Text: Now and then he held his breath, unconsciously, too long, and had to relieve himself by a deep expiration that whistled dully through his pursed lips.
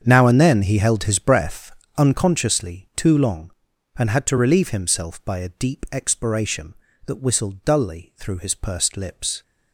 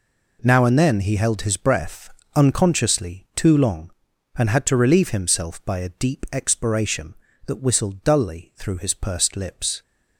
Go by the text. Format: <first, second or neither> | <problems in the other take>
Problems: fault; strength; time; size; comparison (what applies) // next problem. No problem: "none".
second | starts louder than the rest; strong; until 1.8 s; 7 dB